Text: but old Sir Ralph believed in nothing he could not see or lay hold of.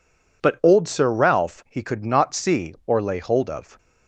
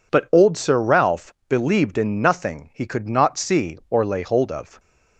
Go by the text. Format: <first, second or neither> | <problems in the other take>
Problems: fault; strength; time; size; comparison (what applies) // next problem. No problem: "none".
second | skips "believed in nothing"; at 1.6 s